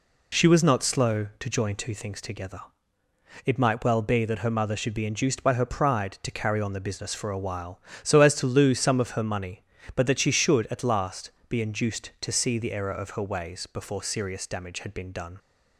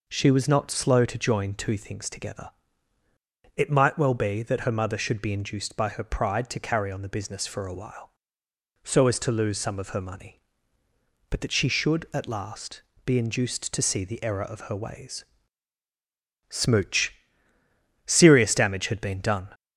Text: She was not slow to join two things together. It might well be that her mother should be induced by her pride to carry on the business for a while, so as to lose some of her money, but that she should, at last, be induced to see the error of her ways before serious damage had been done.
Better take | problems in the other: first | says "smooch" for "before"; at 16.4 s

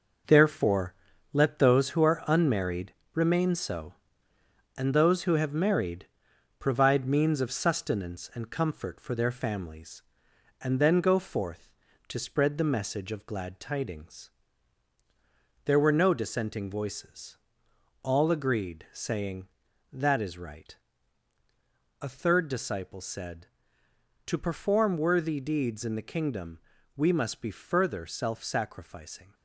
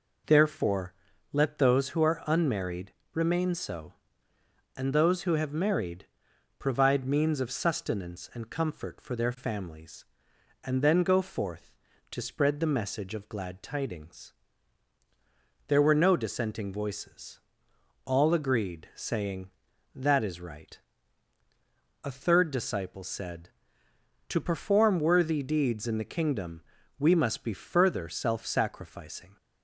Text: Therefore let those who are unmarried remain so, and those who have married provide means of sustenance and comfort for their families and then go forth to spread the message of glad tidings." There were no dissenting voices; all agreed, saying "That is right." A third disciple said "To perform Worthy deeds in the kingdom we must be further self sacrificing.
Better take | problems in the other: second | gets quieter; strong; throughout; 7.5 dB // pauses between "Therefore" and "let"; at 0.9 s; 0.38 s long; also in the second // pauses between "unmarried" and "remain"; slight; at 2.9 s; 0.20 s long; slight in the second // pauses between "married" and "provide"; noticeable; at 6.0 s; 0.52 s long; noticeable in the second // pauses between "kingdom" and "we"; slight; at 26.5 s; 0.36 s long; slight in the second

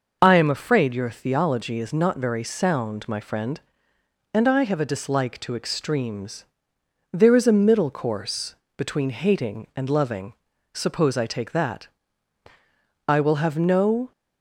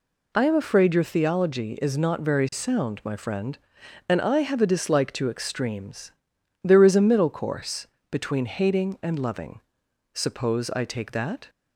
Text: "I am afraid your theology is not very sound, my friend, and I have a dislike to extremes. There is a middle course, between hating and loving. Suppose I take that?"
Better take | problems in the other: second | goes on to say "I will have no"; noticeable; from 13.0 s on; 1.0 s long

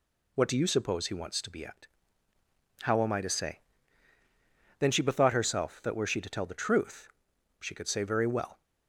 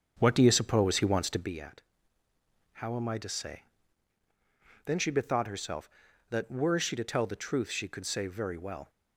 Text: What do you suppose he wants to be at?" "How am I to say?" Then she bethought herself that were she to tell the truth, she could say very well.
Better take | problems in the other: first | starts louder than the rest; until 1.5 s; 7 dB

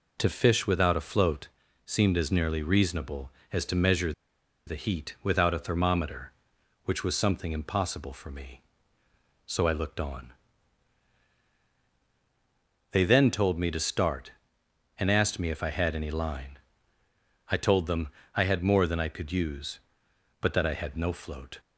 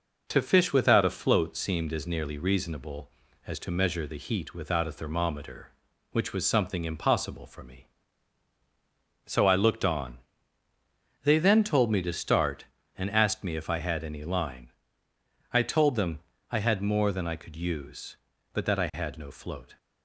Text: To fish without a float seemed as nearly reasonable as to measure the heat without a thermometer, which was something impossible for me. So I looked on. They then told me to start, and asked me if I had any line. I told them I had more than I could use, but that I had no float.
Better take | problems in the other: second | pauses between "float" and "seemed"; at 1.4 s; 0.38 s long // pauses between "measure" and "the"; noticeable; at 4.1 s; 0.55 s long // pauses between "them" and "I"; slight; at 18.0 s; 0.26 s long; slight in the second

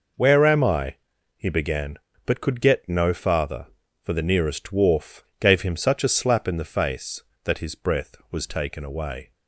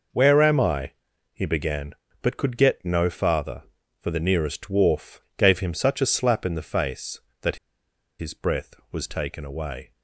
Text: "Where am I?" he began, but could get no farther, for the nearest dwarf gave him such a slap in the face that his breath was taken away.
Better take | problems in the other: first | pauses between "dwarf" and "gave"; slight; at 5.2 s; 0.16 s long; slight in the first // pauses between "that" and "his"; noticeable; at 7.5 s; 0.62 s long

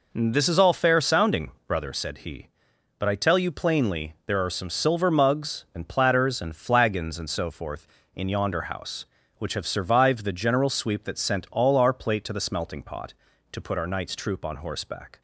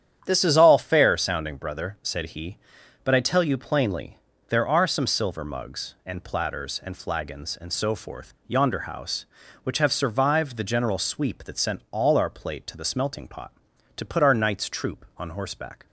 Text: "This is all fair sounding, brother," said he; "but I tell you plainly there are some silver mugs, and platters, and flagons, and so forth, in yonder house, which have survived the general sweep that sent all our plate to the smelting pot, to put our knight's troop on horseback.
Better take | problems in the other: first | starts louder than the rest; strong; until 1.2 s; 9.5 dB // pauses between "plainly" and "there"; slight; at 4.1 s; 0.32 s long // skips "in"; at 8.4 s

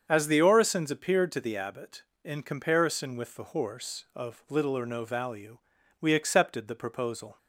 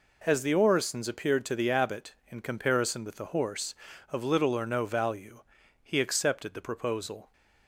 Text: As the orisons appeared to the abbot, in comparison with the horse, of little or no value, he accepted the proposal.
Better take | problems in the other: second | starts louder than the rest; until 1.0 s; 7 dB // says "we" for "he"; at 6.0 s

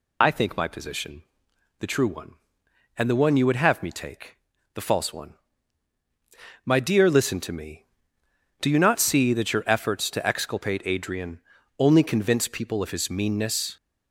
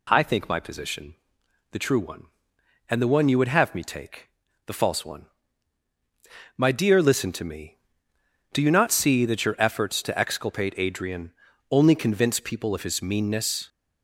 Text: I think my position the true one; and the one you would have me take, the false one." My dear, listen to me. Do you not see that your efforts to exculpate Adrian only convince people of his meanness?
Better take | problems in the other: second | loses the start of "I"; at 0.2 s; 55 ms // pauses between "position" and "the"; noticeable; at 1.2 s; 0.56 s long; noticeable in the second // pauses between "Adrian" and "only"; at 11.4 s; 0.38 s long; also in the second

